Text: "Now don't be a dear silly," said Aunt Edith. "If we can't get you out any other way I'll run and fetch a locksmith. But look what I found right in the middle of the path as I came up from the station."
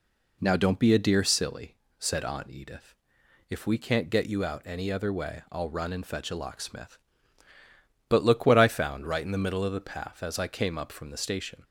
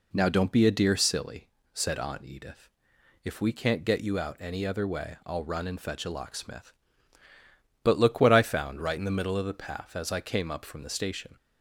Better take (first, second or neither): neither